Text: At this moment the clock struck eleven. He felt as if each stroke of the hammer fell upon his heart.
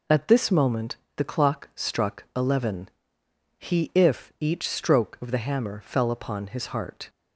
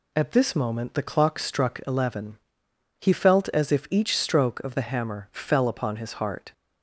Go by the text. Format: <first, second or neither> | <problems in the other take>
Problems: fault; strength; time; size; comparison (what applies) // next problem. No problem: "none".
second | pauses between "moment" and "the"; slight; at 0.9 s; 0.22 s long // skips "felt as"; at 3.9 s